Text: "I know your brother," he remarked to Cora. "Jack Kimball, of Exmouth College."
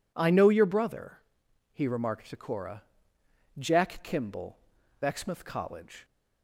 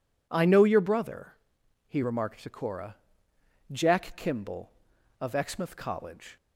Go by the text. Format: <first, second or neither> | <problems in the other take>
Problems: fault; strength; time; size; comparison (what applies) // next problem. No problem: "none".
second | skips "of"; at 4.8 s